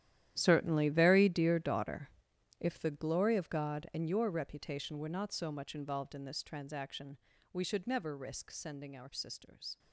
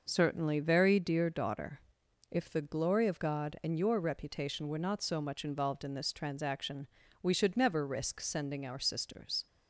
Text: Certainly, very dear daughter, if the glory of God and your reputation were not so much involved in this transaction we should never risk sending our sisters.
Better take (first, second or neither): second